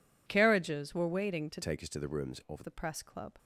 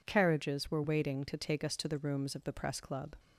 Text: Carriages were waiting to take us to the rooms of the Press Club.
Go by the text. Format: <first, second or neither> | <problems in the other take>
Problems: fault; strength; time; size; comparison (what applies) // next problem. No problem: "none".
second | changes voice from "take" to "of"; from 1.6 to 2.6 s; 1.0 s long